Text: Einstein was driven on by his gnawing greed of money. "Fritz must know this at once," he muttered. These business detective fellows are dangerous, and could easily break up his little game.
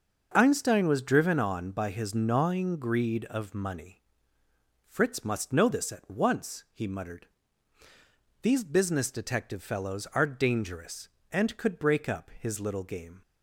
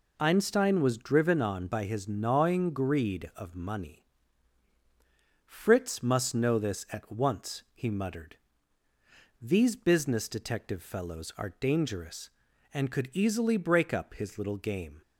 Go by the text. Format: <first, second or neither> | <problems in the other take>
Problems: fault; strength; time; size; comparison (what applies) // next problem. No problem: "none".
second | starts louder than the rest; noticeable; until 1.3 s; 6 dB // skips "easily"; at 11.7 s